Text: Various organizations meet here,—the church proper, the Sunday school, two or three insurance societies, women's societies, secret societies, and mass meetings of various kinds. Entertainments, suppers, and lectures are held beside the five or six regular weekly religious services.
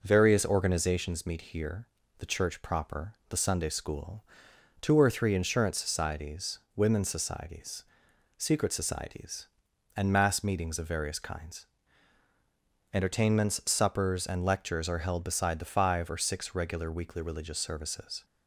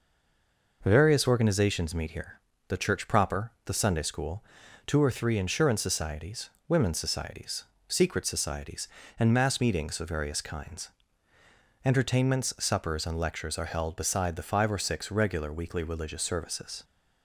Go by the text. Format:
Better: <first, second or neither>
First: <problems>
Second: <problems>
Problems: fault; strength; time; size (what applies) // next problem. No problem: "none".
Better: first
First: none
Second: stays silent before the first word; slight; until 0.8 s; 0.8 s long